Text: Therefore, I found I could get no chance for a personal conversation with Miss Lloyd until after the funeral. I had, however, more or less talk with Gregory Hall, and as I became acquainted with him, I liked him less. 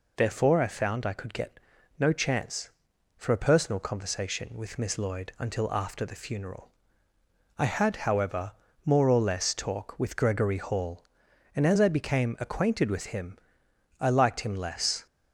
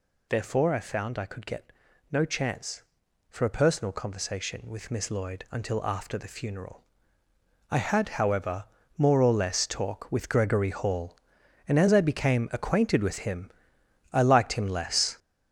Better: first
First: pauses between "get" and "no"; at 1.5 s; 0.40 s long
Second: gets louder; throughout; 7 dB // pauses between "get" and "no"; at 1.7 s; 0.40 s long

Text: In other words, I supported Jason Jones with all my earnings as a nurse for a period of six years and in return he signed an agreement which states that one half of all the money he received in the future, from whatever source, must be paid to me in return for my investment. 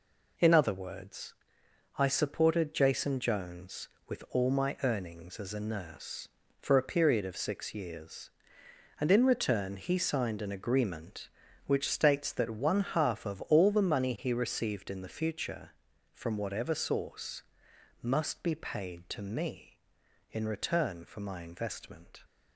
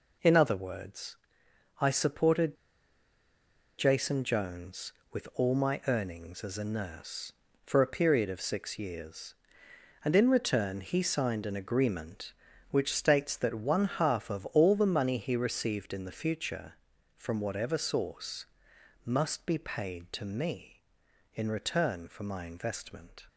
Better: first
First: none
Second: pauses between "supported" and "Jason"; at 2.5 s; 1.2 s long

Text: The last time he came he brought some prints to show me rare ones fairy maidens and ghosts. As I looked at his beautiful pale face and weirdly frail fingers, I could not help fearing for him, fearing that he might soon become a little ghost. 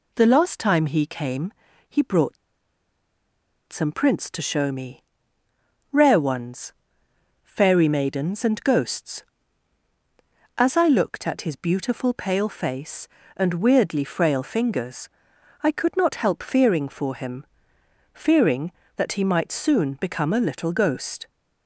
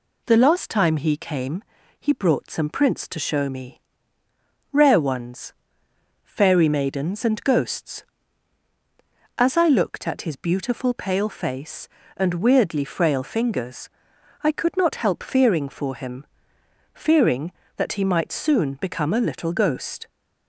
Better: second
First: pauses between "came" and "he"; slight; at 1.5 s; 0.36 s long // pauses between "brought" and "some"; strong; at 2.3 s; 1.3 s long // pauses between "me" and "rare"; noticeable; at 5.0 s; 0.88 s long // pauses between "ones" and "fairy"; noticeable; at 6.7 s; 0.70 s long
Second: pauses between "came" and "he"; slight; at 1.6 s; 0.36 s long // pauses between "me" and "rare"; noticeable; at 3.8 s; 0.90 s long // pauses between "ones" and "fairy"; noticeable; at 5.5 s; 0.70 s long

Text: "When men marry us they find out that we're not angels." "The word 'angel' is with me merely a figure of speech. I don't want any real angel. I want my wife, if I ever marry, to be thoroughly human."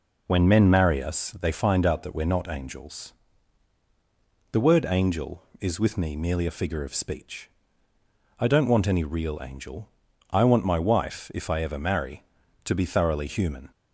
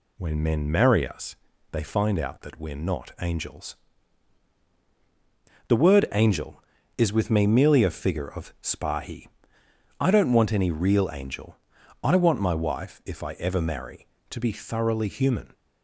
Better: first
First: none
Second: pauses between "us" and "they"; slight; at 1.3 s; 0.36 s long // says "spahi" for "speech"; at 8.6 s

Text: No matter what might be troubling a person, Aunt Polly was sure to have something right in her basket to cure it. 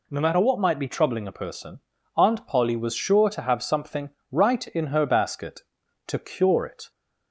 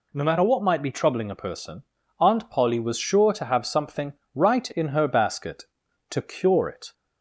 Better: neither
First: pauses between "something" and "right"; slight; at 4.1 s; 0.20 s long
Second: pauses between "something" and "right"; slight; at 4.1 s; 0.20 s long

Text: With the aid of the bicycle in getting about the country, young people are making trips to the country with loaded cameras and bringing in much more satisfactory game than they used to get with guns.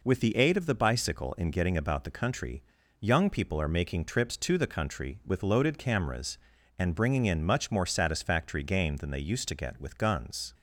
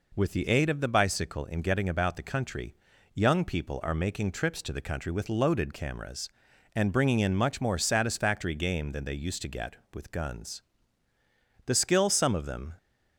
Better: first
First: none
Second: goes on to say "The skill some of them"; noticeable; from 11.6 s on; 1.1 s long

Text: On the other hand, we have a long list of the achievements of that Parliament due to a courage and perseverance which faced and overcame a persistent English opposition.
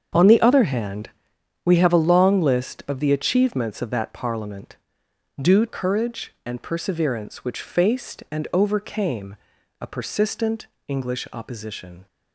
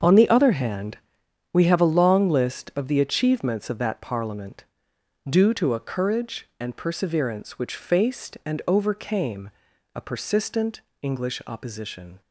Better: second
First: starts louder than the rest; strong; until 1.7 s; 7.5 dB // pauses between "Parliament" and "due"; noticeable; at 4.7 s; 0.66 s long // skips "to a"; at 5.6 s // pauses between "overcame" and "a"; at 9.3 s; 0.44 s long // pauses between "persistent" and "English"; slight; at 10.6 s; 0.22 s long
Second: starts louder than the rest; until 1.6 s; 7 dB // pauses between "Parliament" and "due"; noticeable; at 4.6 s; 0.66 s long // pauses between "overcame" and "a"; at 9.5 s; 0.44 s long // pauses between "persistent" and "English"; slight; at 10.8 s; 0.22 s long

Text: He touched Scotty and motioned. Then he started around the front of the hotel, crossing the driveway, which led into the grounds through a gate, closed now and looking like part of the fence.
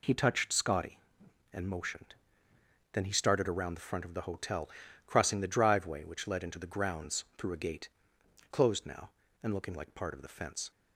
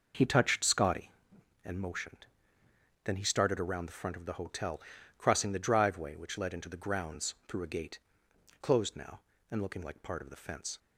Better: first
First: none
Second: starts louder than the rest; noticeable; until 1.3 s; 5.5 dB

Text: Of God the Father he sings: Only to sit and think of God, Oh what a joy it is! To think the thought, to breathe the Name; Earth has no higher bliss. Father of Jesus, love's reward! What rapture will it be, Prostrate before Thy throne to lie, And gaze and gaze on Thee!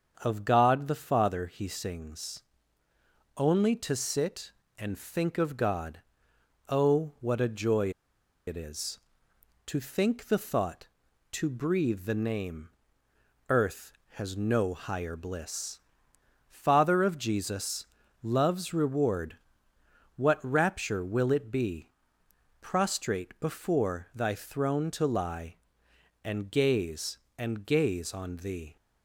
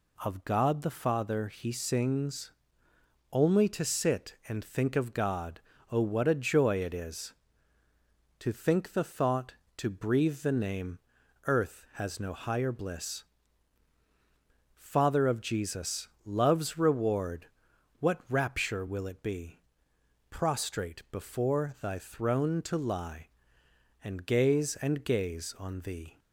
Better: second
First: starts louder than the rest; until 1.2 s; 7 dB // pauses between "joy" and "it"; noticeable; at 7.9 s; 0.55 s long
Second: none

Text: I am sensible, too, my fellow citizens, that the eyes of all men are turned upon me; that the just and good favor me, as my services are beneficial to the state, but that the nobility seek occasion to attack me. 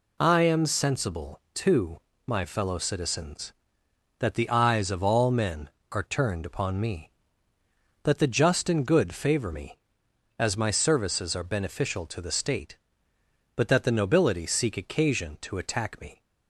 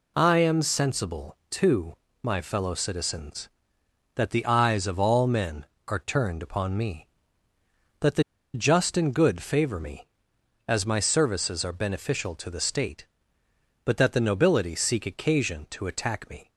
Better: first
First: none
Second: pauses between "the" and "just"; slight; at 8.2 s; 0.32 s long

